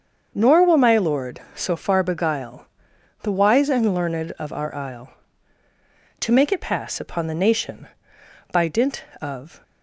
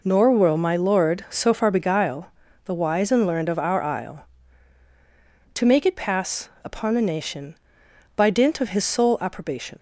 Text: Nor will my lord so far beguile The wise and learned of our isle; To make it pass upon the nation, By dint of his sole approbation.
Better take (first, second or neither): second